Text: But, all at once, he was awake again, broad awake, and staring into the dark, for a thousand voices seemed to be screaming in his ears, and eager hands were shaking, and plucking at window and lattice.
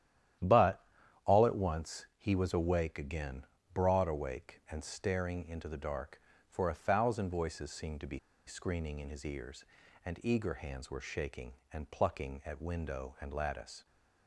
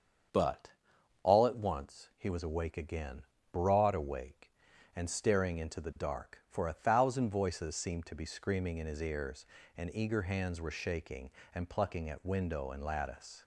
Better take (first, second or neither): second